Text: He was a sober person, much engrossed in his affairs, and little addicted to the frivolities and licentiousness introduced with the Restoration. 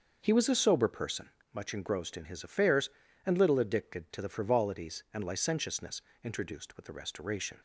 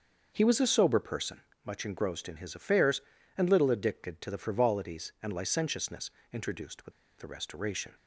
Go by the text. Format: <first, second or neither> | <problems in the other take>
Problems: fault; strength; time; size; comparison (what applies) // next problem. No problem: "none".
first | starts louder than the rest; until 1.3 s; 6 dB; also in the first // pauses between "licentiousness" and "introduced"; slight; at 6.1 s; 0.22 s long; slight in the first // pauses between "with" and "the"; slight; at 6.9 s; 0.27 s long